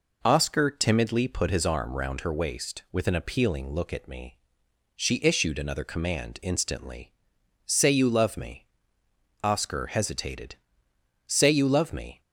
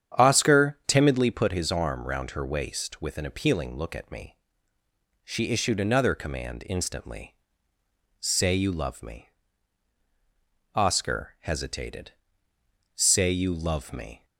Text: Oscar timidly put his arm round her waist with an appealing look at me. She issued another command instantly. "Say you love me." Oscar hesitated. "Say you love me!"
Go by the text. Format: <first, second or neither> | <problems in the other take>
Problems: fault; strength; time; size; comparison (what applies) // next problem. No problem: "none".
first | starts louder than the rest; strong; until 1.1 s; 9 dB